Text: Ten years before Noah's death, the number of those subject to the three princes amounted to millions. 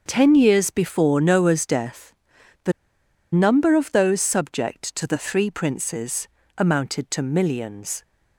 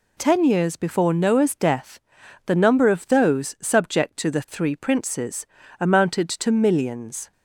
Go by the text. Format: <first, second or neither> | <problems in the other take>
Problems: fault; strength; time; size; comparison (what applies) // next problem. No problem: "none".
second | starts louder than the rest; noticeable; until 1.0 s; 6 dB // pauses between "the" and "number"; noticeable; at 2.7 s; 0.61 s long // pauses between "princes" and "amounted"; slight; at 6.2 s; 0.30 s long; slight in the second